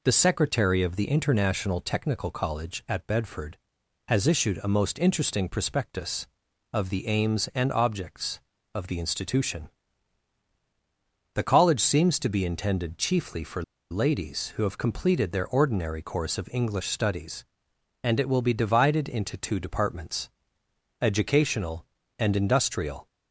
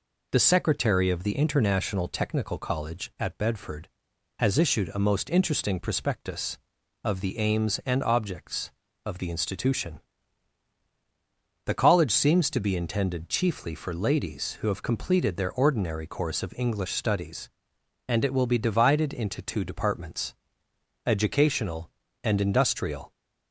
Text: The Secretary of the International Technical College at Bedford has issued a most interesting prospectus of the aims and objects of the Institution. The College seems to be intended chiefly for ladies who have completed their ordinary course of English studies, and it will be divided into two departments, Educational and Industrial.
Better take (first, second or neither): second